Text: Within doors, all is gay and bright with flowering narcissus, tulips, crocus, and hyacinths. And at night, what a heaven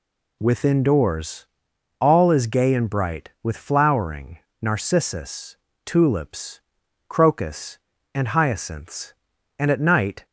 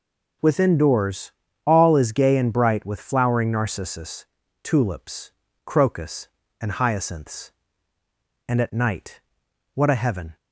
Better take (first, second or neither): second